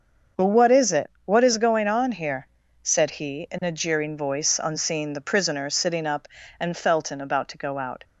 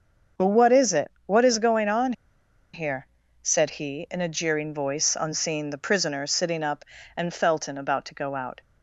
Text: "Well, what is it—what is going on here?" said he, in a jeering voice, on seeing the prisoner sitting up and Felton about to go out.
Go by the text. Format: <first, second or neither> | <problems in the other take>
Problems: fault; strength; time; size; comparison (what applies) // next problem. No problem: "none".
first | starts louder than the rest; until 1.5 s; 6.5 dB; also in the first // pauses between "on" and "here"; noticeable; at 2.1 s; 0.61 s long